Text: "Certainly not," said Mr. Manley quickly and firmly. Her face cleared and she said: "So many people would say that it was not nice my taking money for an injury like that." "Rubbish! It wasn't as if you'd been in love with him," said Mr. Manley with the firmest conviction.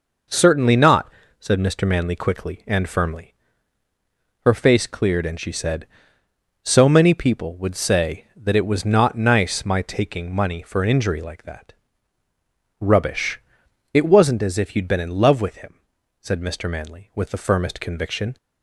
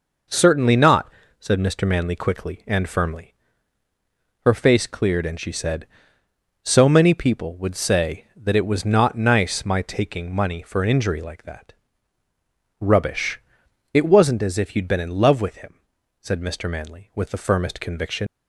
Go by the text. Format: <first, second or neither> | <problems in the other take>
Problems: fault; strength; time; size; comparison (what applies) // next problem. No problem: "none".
first | leaves "conviction" unfinished; at 18.2 s; 100 ms